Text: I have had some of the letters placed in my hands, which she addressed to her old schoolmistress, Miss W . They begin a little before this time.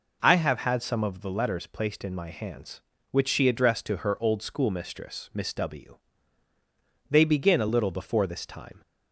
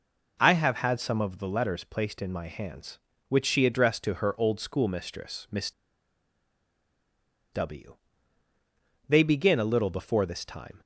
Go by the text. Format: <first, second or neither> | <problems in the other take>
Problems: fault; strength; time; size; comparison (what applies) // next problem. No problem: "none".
first | pauses between "Miss" and "W"; strong; at 5.7 s; 1.8 s long